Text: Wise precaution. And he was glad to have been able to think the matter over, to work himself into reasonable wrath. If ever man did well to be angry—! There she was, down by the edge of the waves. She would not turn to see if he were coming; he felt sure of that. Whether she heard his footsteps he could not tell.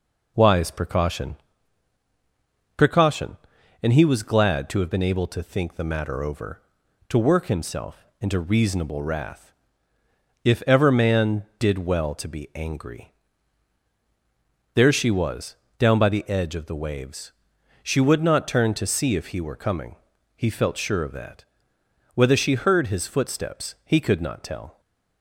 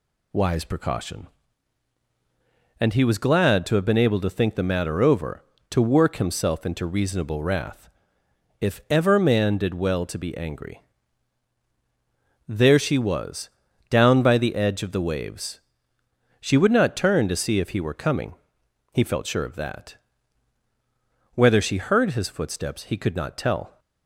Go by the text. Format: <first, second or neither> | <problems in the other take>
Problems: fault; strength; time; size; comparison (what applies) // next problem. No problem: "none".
second | says "precaution" twice; at 2.7 s // pauses between "himself" and "into"; slight; at 8.0 s; 0.16 s long